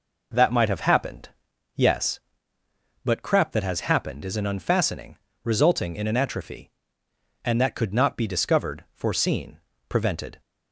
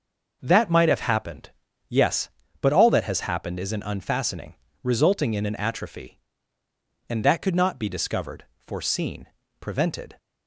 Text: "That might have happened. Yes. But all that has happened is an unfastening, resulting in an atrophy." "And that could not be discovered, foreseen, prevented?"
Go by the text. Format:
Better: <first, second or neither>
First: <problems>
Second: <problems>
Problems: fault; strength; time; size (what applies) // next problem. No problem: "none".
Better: second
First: says "crap" for "all"; at 3.2 s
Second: none